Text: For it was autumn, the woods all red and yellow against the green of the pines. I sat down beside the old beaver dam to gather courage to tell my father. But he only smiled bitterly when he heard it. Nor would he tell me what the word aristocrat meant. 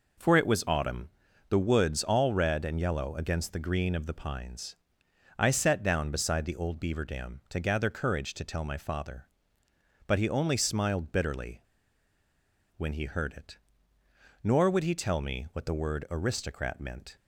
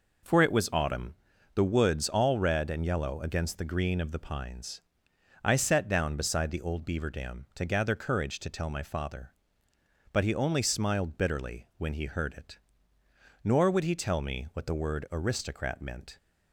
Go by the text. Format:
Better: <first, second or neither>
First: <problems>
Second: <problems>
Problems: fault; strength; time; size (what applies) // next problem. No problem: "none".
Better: second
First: pauses between "bitterly" and "when"; at 11.6 s; 1.1 s long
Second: none